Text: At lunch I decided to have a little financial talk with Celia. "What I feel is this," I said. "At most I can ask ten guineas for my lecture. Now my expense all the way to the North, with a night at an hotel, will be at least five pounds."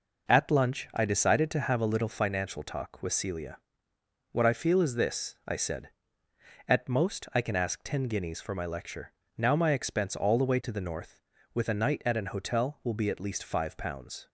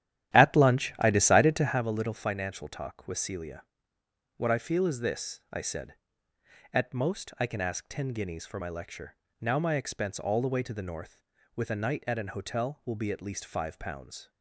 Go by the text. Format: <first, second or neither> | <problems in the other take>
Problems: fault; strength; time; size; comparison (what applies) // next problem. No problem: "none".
first | starts louder than the rest; strong; until 1.8 s; 12 dB